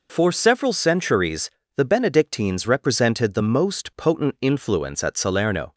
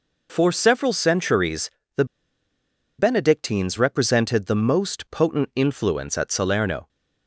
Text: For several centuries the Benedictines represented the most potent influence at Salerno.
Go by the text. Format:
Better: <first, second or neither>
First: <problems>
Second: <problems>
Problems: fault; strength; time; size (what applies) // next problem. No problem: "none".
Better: first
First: pauses between "centuries" and "the"; slight; at 1.4 s; 0.28 s long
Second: pauses between "centuries" and "the"; slight; at 1.6 s; 0.28 s long // pauses between "the" and "Benedictines"; noticeable; at 2.0 s; 0.93 s long